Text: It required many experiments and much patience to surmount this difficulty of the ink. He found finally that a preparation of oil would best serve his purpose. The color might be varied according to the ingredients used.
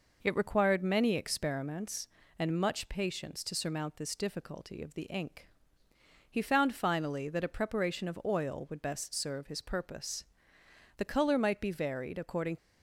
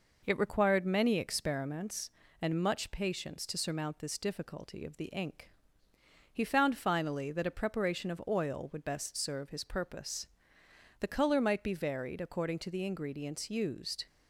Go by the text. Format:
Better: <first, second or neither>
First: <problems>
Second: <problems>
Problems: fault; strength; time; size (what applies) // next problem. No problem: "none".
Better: second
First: stops before "to the ingredients used"; at 12.5 s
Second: none